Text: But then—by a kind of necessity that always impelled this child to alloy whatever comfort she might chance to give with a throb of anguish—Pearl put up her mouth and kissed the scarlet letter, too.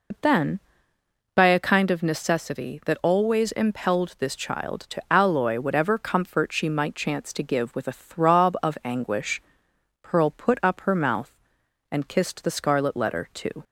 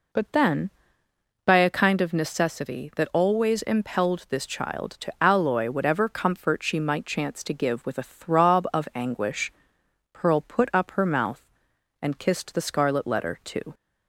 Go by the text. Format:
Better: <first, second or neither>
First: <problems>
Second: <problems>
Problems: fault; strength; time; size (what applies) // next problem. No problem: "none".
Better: second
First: loses the start of "But"; at 0.1 s; 70 ms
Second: none